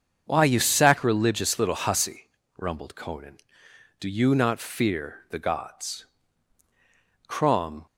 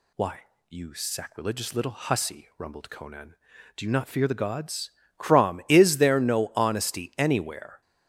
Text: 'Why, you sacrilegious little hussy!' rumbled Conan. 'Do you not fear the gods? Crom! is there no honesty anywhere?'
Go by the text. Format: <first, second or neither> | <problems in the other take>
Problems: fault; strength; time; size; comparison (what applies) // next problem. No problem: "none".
second | starts louder than the rest; until 1.2 s; 7 dB // stops before "is there no honesty anywhere"; at 7.8 s